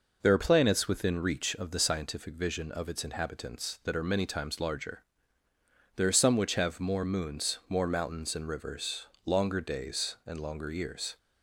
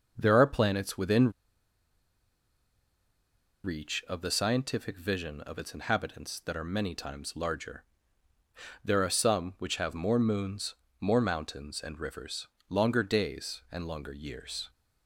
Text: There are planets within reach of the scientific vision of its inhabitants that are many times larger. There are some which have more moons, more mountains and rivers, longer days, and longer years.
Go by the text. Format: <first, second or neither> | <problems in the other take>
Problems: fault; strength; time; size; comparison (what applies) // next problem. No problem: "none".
first | starts louder than the rest; noticeable; until 1.1 s; 6 dB // pauses between "within" and "reach"; strong; at 1.3 s; 2.3 s long